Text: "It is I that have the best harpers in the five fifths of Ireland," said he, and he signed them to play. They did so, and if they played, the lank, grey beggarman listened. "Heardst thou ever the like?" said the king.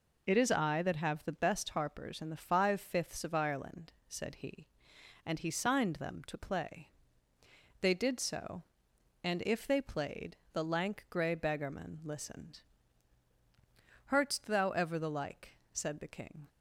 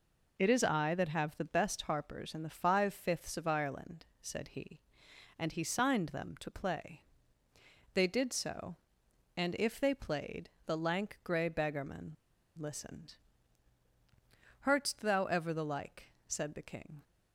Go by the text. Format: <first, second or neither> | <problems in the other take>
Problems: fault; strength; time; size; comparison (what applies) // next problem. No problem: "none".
first | pauses between "beggarman" and "listened"; at 12.1 s; 0.42 s long